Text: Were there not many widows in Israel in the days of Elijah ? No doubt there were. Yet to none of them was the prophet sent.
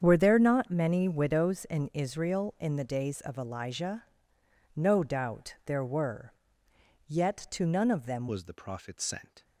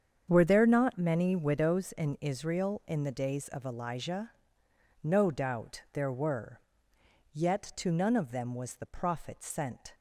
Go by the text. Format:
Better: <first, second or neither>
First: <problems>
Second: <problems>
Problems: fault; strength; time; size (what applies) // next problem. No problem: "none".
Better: second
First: starts louder than the rest; strong; until 1.0 s; 7.5 dB // changes voice at "was"; from 8.2 s on; 1.2 s long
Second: starts louder than the rest; strong; until 1.2 s; 7.5 dB